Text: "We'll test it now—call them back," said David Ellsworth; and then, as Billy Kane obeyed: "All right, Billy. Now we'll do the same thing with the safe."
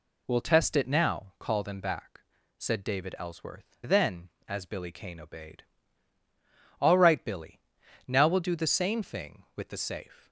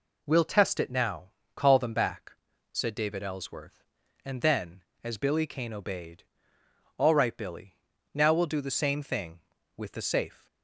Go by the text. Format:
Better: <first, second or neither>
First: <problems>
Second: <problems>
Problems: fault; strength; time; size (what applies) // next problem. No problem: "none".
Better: second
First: skips "and"; at 3.8 s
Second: none